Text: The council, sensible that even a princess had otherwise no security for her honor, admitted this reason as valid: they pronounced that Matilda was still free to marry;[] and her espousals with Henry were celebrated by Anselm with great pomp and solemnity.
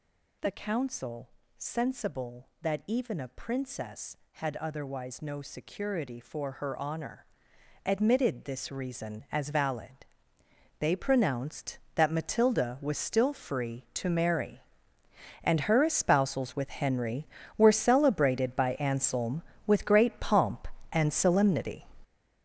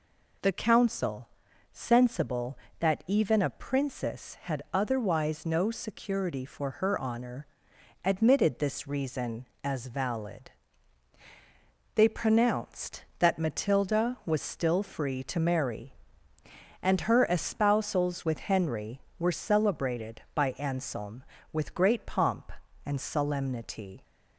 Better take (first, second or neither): second